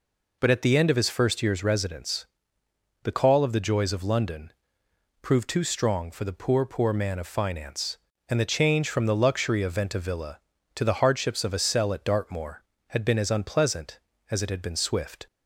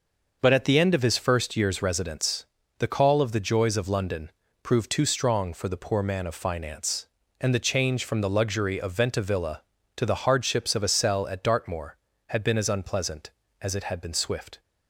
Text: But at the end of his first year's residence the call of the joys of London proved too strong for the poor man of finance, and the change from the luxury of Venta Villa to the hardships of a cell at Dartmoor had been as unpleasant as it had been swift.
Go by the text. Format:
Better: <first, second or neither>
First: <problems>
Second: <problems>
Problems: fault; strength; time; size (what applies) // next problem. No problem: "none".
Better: second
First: pauses between "residence" and "the"; noticeable; at 2.2 s; 0.76 s long // pauses between "London" and "proved"; noticeable; at 4.5 s; 0.72 s long // says "poor" twice; at 6.6 s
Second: pauses between "residence" and "the"; slight; at 2.4 s; 0.32 s long // pauses between "London" and "proved"; slight; at 4.3 s; 0.32 s long